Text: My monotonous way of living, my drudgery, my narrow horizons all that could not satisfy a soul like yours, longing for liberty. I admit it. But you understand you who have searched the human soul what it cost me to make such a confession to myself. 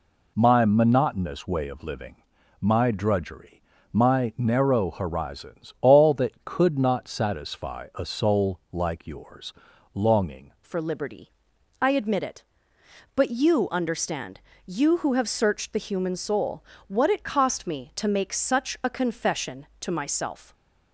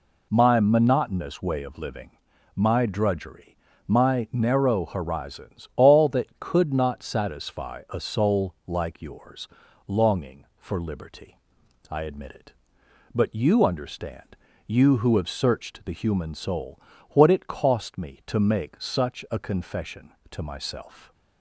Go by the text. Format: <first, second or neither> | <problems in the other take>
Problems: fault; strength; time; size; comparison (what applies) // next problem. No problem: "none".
second | changes voice at "for"; from 10.6 s on; 9.9 s long // pauses between "understand" and "you"; slight; at 14.3 s; 0.28 s long; slight in the second // pauses between "soul" and "what"; slight; at 16.6 s; 0.26 s long; slight in the second // stays silent after the last word; slight; from 20.4 s on; 0.5 s long